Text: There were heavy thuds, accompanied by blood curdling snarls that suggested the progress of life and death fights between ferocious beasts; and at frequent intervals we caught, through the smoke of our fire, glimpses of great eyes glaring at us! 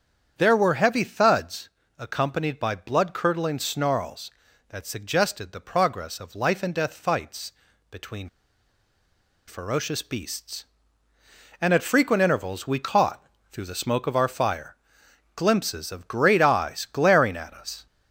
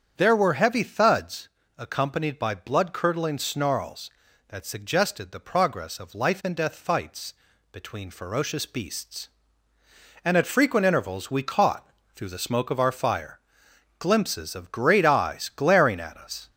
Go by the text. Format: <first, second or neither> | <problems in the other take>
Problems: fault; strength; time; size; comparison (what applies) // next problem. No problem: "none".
second | starts louder than the rest; strong; until 1.3 s; 8 dB; strong in the second // pauses between "fights" and "between"; at 7.5 s; 0.38 s long; also in the second // pauses between "between" and "ferocious"; at 8.2 s; 1.1 s long